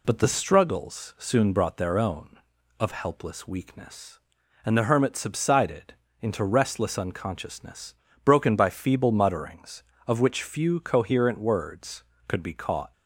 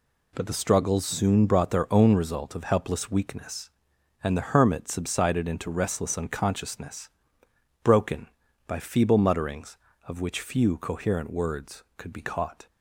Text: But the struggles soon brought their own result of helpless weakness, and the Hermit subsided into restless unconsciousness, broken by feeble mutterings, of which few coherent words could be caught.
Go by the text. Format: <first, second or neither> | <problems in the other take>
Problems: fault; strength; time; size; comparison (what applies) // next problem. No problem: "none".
second | skips "result"; at 2.5 s // pauses between "subsided" and "into"; slight; at 5.9 s; 0.28 s long